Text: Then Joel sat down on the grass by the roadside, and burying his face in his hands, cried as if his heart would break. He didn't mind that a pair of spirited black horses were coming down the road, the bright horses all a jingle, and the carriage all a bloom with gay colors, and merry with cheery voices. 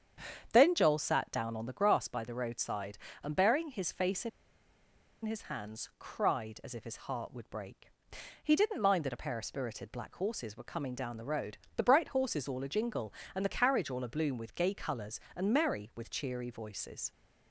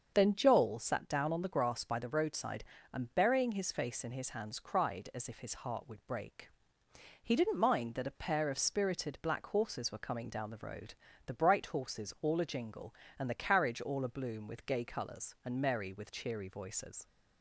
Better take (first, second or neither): second